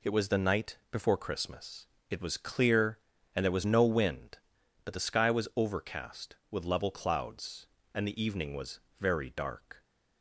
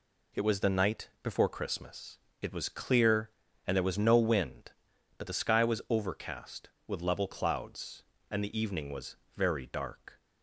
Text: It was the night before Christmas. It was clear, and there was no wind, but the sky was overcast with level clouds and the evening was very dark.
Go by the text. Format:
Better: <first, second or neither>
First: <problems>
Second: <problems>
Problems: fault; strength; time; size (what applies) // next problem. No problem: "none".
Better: neither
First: pauses between "was" and "very"; slight; at 8.8 s; 0.20 s long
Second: pauses between "was" and "very"; slight; at 9.1 s; 0.20 s long